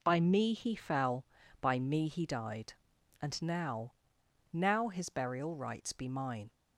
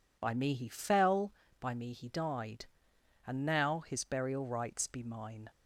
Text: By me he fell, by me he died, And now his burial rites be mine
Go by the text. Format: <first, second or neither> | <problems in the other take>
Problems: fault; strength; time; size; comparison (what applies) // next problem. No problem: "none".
second | says "now" twice; at 4.5 s